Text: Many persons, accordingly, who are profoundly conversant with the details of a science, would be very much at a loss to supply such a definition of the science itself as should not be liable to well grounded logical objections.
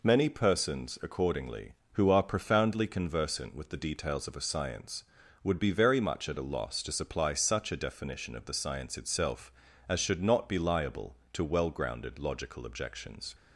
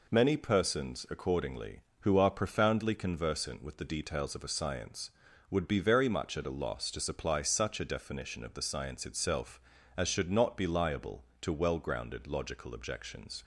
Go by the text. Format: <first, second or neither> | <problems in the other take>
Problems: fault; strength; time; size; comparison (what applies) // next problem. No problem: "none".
neither | none